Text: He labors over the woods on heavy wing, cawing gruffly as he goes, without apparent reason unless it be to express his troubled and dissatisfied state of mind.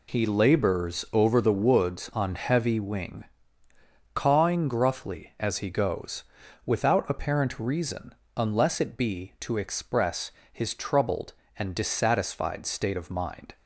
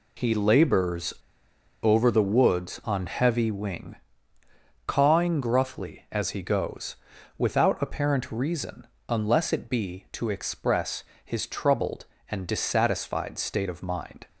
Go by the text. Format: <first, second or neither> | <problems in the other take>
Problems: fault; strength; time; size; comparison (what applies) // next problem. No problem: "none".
first | pauses between "labors" and "over"; noticeable; at 1.1 s; 0.69 s long // pauses between "reason" and "unless"; slight; at 8.8 s; 0.22 s long; slight in the first // pauses between "express" and "his"; slight; at 11.0 s; 0.22 s long; slight in the first